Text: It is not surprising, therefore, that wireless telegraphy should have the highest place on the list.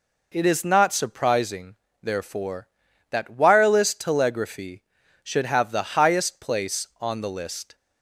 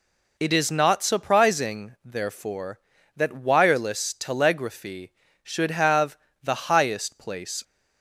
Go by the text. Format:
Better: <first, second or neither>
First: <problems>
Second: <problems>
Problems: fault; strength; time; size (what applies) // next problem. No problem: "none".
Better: first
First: none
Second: pauses between "have" and "the"; slight; at 6.1 s; 0.28 s long // stops before "on the list"; at 7.6 s